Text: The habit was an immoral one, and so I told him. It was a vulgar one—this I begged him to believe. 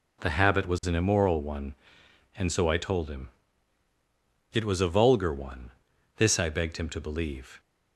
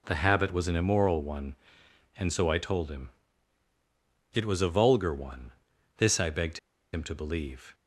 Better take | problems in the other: first | pauses between "begged" and "him"; slight; at 6.5 s; 0.34 s long

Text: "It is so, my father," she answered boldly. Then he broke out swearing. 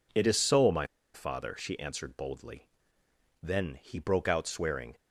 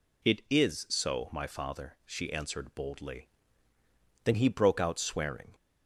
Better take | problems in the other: second | pauses between "my" and "father"; slight; at 0.8 s; 0.27 s long

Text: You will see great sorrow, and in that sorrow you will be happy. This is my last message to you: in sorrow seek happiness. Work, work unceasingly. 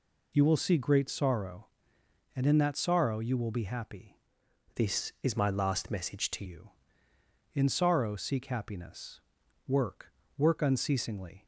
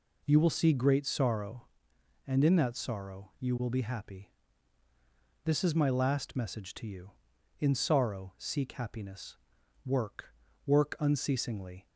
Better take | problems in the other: second | changes voice from "This" to "to"; from 4.7 to 6.4 s; 1.7 s long

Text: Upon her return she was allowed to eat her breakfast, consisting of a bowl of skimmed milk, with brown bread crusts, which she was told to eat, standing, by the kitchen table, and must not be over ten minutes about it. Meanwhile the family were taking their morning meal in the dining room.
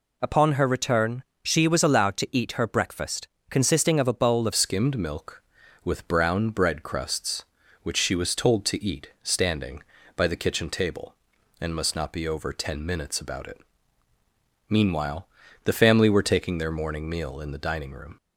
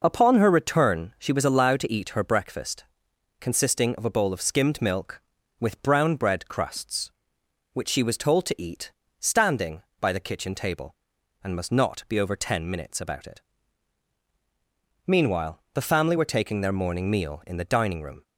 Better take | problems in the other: second | pauses between "return" and "she"; slight; at 1.2 s; 0.20 s long // changes voice at "skimmed"; from 4.5 s on; 13.6 s long // pauses between "Meanwhile" and "the"; slight; at 15.2 s; 0.36 s long

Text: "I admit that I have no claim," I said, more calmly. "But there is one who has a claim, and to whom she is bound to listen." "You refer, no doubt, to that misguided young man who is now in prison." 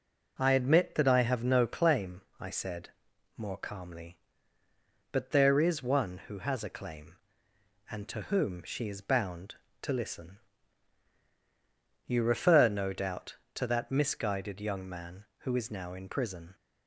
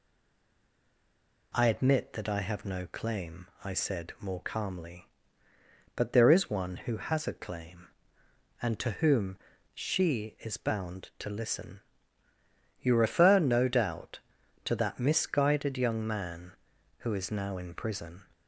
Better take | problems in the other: first | stays silent before the first word; noticeable; until 1.5 s; 1.5 s long // pauses between "whom" and "she"; slight; at 9.3 s; 0.36 s long

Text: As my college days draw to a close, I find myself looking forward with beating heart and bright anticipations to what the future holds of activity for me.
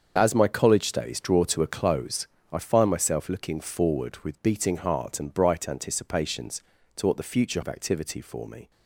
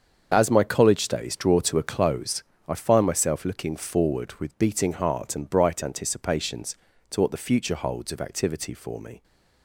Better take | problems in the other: second | starts louder than the rest; until 1.1 s; 7 dB; also in the second // skips "holds"; at 7.6 s

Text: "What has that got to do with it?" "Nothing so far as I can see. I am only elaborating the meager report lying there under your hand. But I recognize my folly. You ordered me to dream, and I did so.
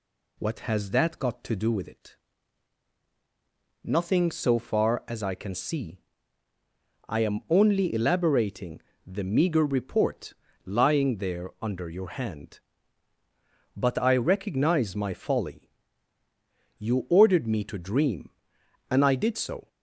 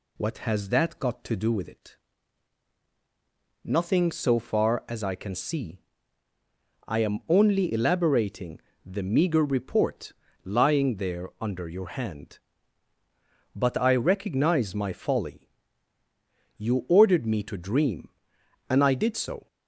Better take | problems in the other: neither | pauses between "elaborating" and "the"; slight; the same in both // pauses between "report" and "lying"; slight; the same in both

